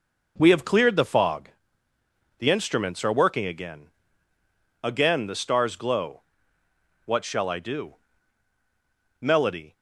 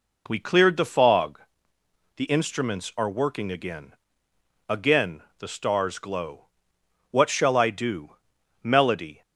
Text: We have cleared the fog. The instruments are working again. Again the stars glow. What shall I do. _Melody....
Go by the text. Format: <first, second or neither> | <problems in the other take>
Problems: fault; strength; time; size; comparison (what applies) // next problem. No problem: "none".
first | skips "have"; at 0.4 s // pauses between "Again" and "the"; slight; at 5.2 s; 0.16 s long